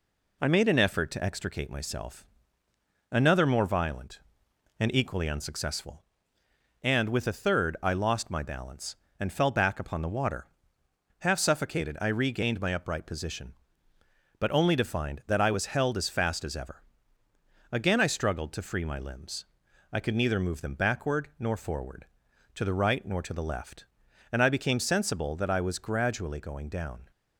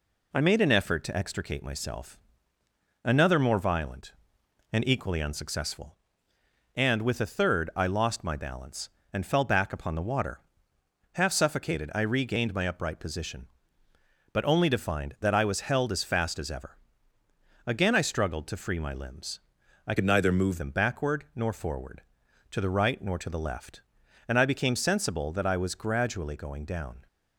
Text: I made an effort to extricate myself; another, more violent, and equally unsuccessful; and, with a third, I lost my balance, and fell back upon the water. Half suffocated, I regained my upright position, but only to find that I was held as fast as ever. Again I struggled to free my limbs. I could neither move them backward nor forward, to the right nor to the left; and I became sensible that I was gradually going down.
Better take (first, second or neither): first